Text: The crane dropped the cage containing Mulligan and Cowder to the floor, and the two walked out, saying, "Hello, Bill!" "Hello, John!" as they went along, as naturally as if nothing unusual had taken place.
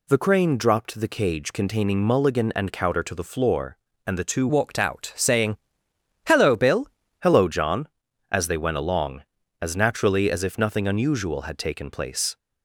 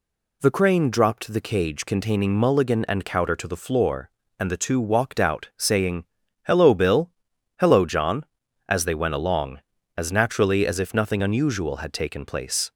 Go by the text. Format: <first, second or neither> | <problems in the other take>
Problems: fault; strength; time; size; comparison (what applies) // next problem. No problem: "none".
second | changes voice from "walked" to "Bill"; from 4.4 to 6.8 s; 2.4 s long